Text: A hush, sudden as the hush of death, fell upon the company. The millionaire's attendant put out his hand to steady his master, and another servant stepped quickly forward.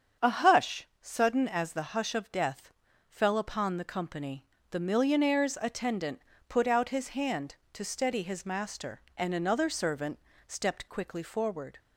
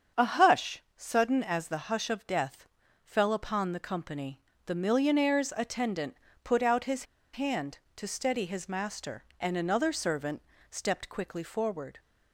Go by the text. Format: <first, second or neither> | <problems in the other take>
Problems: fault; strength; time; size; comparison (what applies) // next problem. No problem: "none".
first | starts louder than the rest; strong; until 1.3 s; 7.5 dB; strong in the first // pauses between "attendant" and "put"; slight; at 6.1 s; 0.26 s long; slight in the first // pauses between "his" and "hand"; slight; at 7.0 s; 0.30 s long // pauses between "servant" and "stepped"; slight; at 10.4 s; 0.30 s long; slight in the first